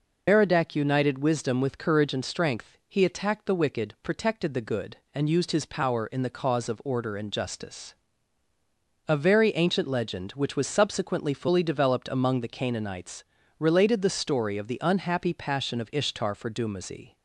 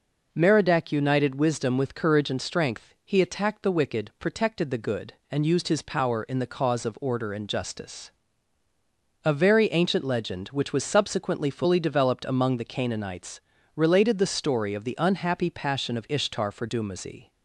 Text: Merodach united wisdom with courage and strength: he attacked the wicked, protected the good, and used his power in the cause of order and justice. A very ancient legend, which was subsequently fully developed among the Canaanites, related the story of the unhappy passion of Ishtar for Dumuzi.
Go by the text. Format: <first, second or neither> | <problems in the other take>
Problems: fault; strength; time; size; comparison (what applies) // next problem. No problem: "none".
second | loses the start of "Merodach"; at 0.2 s; 115 ms